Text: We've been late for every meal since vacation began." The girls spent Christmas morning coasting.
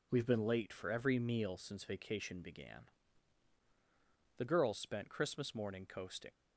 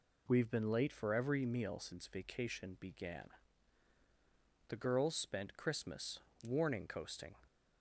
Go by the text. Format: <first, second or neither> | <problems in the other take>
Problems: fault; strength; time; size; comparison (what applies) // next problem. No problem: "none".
first | says "warning" for "morning"; at 6.4 s